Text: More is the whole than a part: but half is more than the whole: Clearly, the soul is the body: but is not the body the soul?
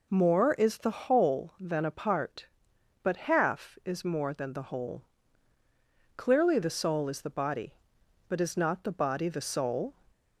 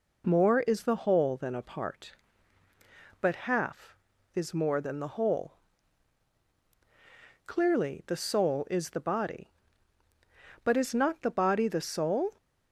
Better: neither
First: none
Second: none

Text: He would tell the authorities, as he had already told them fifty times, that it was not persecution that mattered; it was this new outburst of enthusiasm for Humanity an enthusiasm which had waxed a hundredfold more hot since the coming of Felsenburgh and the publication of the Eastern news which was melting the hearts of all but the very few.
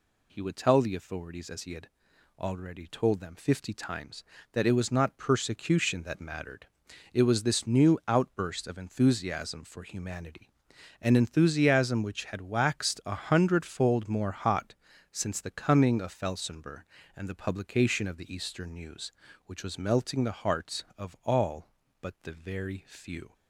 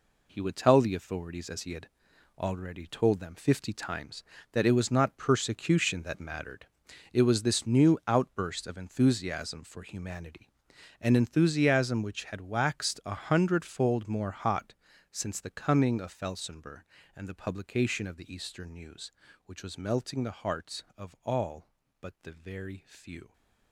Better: first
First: pauses between "had" and "already"; noticeable; at 1.8 s; 0.50 s long // pauses between "Humanity" and "an"; noticeable; at 10.4 s; 0.54 s long // pauses between "hot" and "since"; slight; at 14.7 s; 0.36 s long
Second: gets quieter; strong; throughout; 9 dB // pauses between "had" and "already"; noticeable; at 1.8 s; 0.50 s long // pauses between "Humanity" and "an"; noticeable; at 10.4 s; 0.54 s long // pauses between "hot" and "since"; slight; at 14.7 s; 0.36 s long

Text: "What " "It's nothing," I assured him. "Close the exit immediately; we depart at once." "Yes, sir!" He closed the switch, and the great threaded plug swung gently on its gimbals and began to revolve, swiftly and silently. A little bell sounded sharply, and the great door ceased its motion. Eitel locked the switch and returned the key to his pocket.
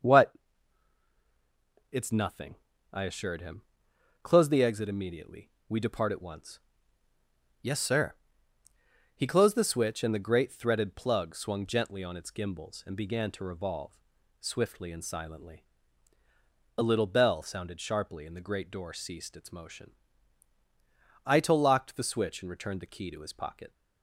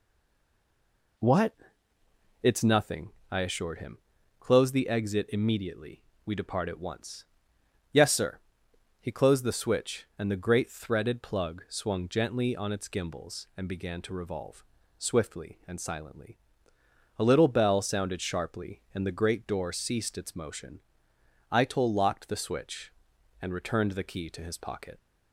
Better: first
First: none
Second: stays silent before the first word; noticeable; until 1.1 s; 1.1 s long

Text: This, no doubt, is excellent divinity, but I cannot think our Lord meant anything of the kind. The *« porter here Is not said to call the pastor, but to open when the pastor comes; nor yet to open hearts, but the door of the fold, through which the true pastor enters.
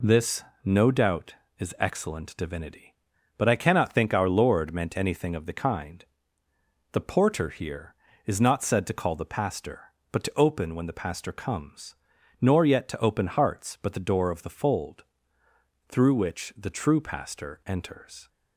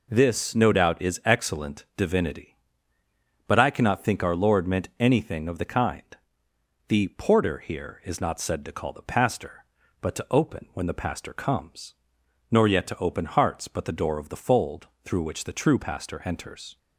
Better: neither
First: none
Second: none

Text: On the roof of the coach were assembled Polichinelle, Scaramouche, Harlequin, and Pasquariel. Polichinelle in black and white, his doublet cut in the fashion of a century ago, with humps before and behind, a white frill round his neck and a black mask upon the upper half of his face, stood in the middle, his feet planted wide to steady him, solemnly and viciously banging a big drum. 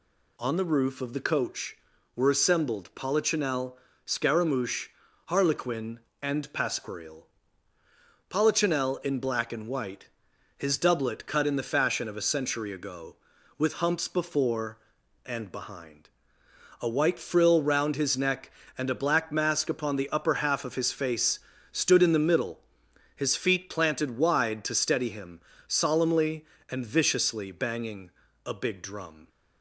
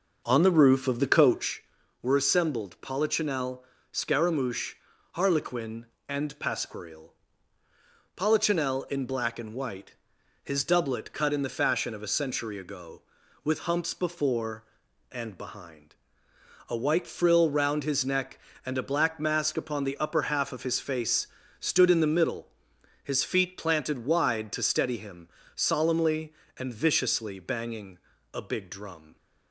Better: first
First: pauses between "banging" and "a"; slight; at 28.0 s; 0.36 s long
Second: starts louder than the rest; noticeable; until 1.5 s; 6 dB // pauses between "banging" and "a"; slight; at 27.9 s; 0.36 s long

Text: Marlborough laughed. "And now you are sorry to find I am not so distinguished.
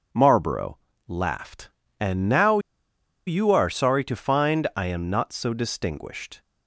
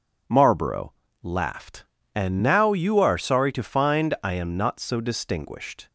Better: second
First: pauses between "Marlborough" and "laughed"; slight; at 0.7 s; 0.28 s long // pauses between "now" and "you"; noticeable; at 2.5 s; 0.68 s long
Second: pauses between "Marlborough" and "laughed"; slight; at 0.9 s; 0.28 s long

